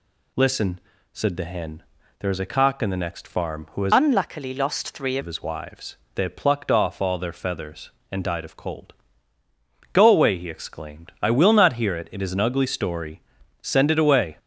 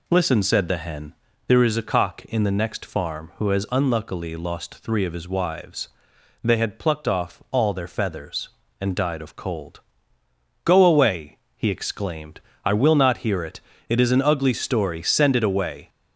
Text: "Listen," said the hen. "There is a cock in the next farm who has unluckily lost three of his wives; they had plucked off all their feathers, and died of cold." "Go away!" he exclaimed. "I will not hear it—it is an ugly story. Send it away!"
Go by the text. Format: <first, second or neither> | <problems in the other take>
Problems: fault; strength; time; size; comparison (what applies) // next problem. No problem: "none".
second | changes voice from "unluckily" to "three"; from 3.9 to 5.1 s; 1.2 s long